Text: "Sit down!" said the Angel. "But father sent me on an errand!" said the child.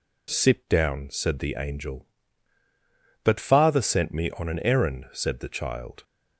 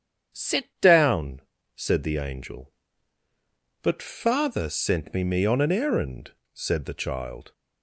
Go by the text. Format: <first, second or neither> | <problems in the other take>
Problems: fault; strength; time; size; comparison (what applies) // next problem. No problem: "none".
first | starts louder than the rest; strong; until 1.7 s; 8 dB // says "me" twice; at 5.2 s